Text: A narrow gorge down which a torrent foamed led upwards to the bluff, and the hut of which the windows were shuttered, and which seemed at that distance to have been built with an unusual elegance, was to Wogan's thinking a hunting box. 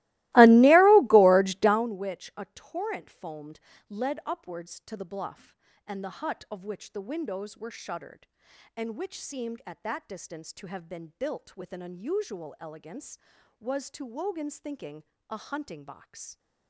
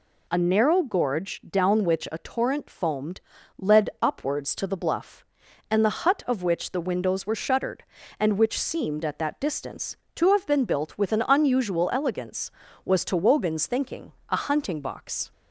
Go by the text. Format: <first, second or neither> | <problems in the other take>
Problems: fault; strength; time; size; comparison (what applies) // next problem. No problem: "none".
second | starts louder than the rest; strong; until 1.9 s; 19.5 dB // pauses between "foamed" and "led"; slight; at 3.6 s; 0.30 s long; slight in the second // pauses between "thinking" and "a"; slight; at 15.0 s; 0.26 s long; slight in the second